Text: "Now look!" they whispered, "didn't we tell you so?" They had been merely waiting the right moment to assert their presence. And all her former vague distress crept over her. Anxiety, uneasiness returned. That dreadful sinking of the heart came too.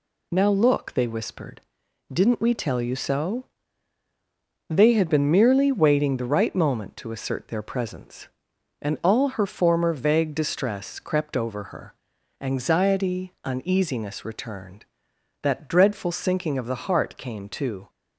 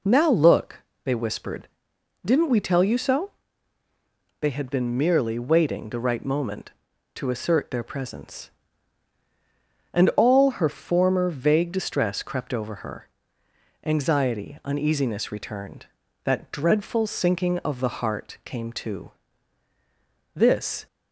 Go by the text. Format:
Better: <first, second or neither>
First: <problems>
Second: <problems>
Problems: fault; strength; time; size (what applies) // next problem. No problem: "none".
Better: first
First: none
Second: goes on to say "This"; from 20.3 s on; 0.52 s long